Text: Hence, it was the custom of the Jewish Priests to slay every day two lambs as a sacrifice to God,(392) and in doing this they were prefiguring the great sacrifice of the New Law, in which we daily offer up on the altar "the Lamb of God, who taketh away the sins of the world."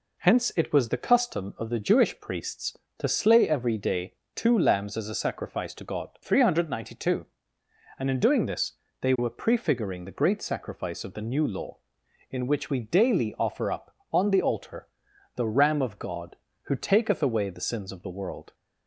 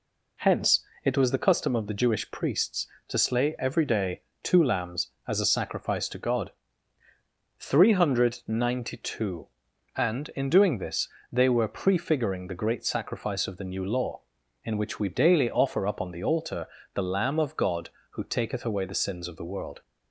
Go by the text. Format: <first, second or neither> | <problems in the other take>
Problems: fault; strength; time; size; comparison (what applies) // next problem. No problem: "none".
second | pauses between "day" and "two"; slight; at 4.1 s; 0.20 s long; slight in the second // pauses between "this" and "they"; slight; at 8.7 s; 0.24 s long; slight in the second // pauses between "altar" and "the"; noticeable; at 14.8 s; 0.48 s long; slight in the second // says "Ram" for "Lamb"; at 15.4 s